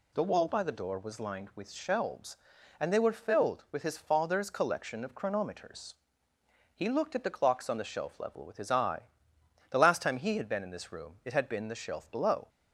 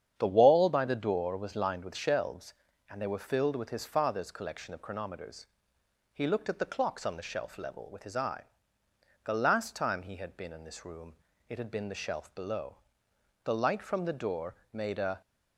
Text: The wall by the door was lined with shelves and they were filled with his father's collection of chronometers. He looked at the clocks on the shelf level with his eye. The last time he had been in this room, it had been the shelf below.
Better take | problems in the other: first | starts louder than the rest; strong; until 1.1 s; 8.5 dB // goes on to say "The light from the door made a"; strong; from 13.4 s on; 1.7 s long

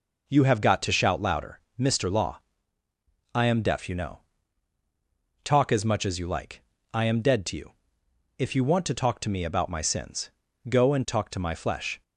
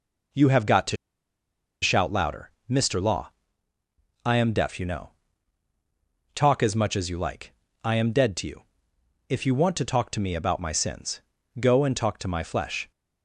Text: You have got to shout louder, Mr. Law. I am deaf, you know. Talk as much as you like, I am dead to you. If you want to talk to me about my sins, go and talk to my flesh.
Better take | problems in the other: first | pauses between "to" and "shout"; noticeable; at 0.9 s; 0.86 s long

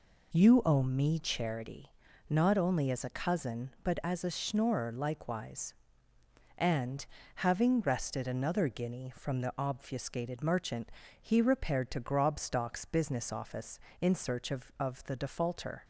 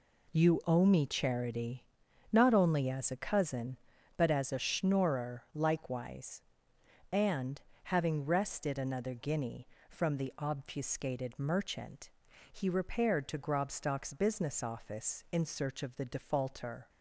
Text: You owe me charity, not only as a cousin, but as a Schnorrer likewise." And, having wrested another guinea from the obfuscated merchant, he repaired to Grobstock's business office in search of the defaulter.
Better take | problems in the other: second | says "of" twice; at 14.8 s

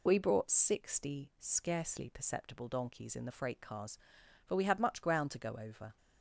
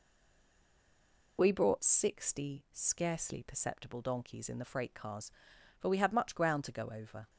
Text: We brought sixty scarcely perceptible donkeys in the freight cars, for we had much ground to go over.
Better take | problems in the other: first | stays silent before the first word; noticeable; until 1.3 s; 1.3 s long

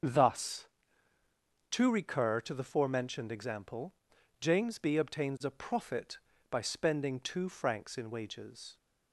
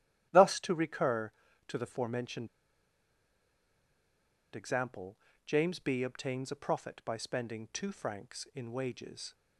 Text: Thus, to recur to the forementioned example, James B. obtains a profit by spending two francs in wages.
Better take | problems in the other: first | starts louder than the rest; strong; until 1.6 s; 12.5 dB; also in the first // pauses between "forementioned" and "example"; strong; at 2.4 s; 2.0 s long

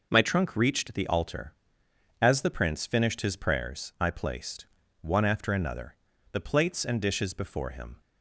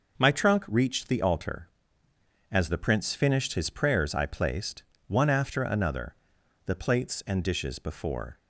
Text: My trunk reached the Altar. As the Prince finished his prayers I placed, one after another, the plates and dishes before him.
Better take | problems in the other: first | stops before "him"; at 8.3 s

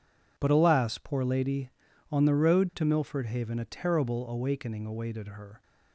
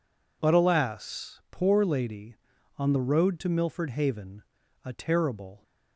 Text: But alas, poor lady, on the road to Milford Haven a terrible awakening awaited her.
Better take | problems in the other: first | pauses between "Haven" and "a"; at 4.4 s; 0.42 s long // stops before "awakening awaited her"; at 5.6 s

